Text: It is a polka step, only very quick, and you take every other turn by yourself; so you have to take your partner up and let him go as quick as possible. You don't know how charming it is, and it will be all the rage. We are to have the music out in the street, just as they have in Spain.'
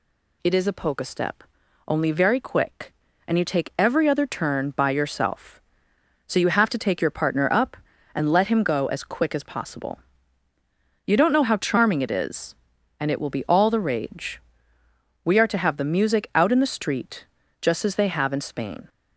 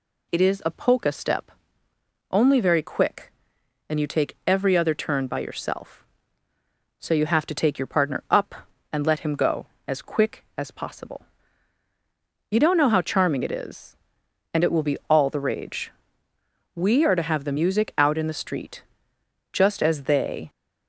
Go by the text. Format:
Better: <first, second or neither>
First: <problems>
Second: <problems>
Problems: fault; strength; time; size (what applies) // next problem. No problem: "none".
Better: first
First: none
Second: stops before "have in Spain"; at 20.4 s